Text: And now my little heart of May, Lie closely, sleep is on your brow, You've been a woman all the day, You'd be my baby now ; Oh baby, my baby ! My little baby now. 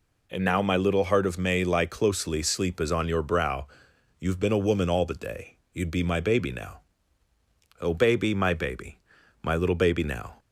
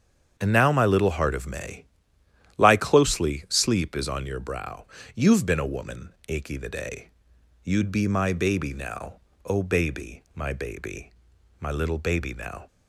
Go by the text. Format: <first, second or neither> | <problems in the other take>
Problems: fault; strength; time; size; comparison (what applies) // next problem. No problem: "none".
first | starts louder than the rest; strong; until 1.3 s; 7.5 dB // says "achy" for "all"; at 6.2 s